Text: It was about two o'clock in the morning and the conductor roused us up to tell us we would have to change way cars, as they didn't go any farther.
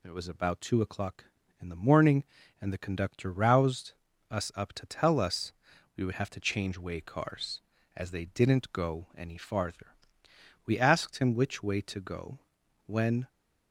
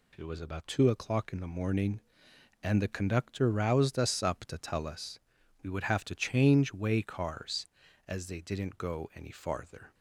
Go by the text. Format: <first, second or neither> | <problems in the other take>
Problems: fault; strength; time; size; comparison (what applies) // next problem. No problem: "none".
second | pauses between "roused" and "us"; at 3.9 s; 0.38 s long // pauses between "us" and "we"; at 5.5 s; 0.44 s long; also in the second // goes on to say "We asked him which way to go when"; strong; from 10.6 s on; 2.6 s long